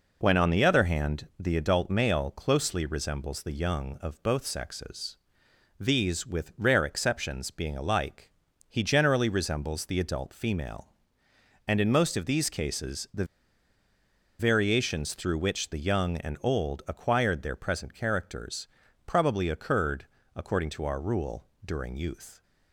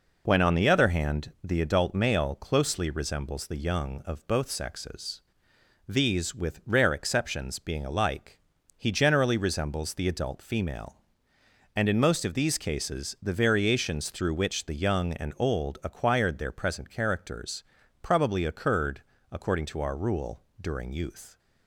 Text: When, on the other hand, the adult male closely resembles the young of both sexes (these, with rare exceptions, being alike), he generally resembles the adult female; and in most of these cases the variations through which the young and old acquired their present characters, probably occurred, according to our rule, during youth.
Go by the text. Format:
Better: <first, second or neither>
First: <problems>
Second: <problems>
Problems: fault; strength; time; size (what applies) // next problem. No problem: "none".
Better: second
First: pauses between "the" and "variations"; at 13.2 s; 1.1 s long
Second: none